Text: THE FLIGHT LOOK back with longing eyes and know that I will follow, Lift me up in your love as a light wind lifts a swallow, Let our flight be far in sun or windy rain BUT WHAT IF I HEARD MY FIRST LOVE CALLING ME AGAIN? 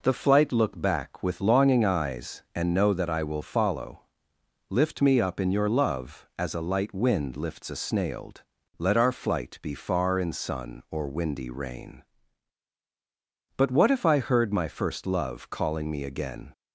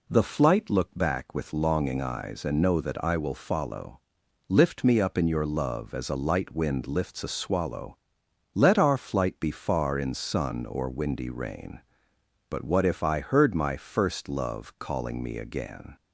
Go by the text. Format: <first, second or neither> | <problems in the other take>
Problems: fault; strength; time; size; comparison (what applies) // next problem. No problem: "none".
second | says "snailed" for "swallow"; at 7.7 s